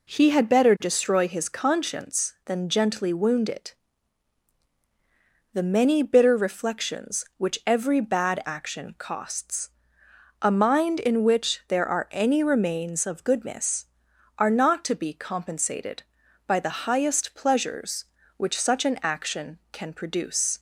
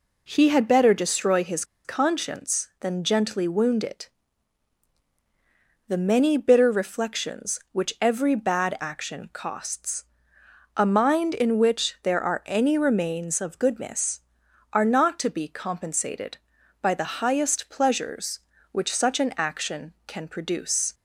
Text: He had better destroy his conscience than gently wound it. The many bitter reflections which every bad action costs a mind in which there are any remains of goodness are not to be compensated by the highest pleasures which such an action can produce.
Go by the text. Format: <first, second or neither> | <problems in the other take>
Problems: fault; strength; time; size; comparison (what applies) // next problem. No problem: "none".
first | pauses between "his" and "conscience"; slight; at 1.6 s; 0.21 s long // pauses between "costs" and "a"; noticeable; at 10.0 s; 0.72 s long; noticeable in the first